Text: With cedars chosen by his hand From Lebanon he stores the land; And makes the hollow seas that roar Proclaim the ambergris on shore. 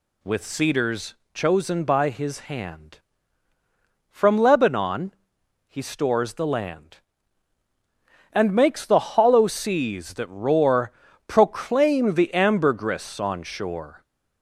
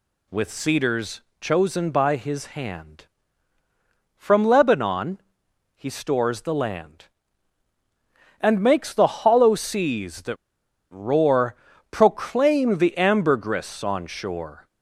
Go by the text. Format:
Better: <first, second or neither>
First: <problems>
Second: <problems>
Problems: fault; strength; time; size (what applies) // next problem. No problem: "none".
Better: first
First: pauses between "cedars" and "chosen"; slight; at 1.1 s; 0.18 s long // pauses between "Lebanon" and "he"; noticeable; at 5.1 s; 0.50 s long // pauses between "roar" and "Proclaim"; at 10.9 s; 0.38 s long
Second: pauses between "cedars" and "chosen"; slight; at 1.2 s; 0.18 s long // pauses between "Lebanon" and "he"; noticeable; at 5.2 s; 0.52 s long // pauses between "that" and "roar"; noticeable; at 10.3 s; 0.55 s long // pauses between "roar" and "Proclaim"; at 11.5 s; 0.38 s long